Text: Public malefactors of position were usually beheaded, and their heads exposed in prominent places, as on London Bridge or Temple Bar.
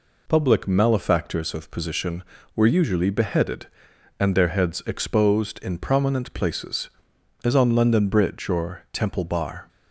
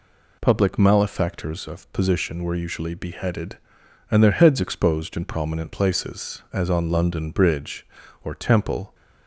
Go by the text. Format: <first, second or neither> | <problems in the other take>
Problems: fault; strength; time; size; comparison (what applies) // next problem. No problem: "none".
first | stops before "Bar"; at 8.9 s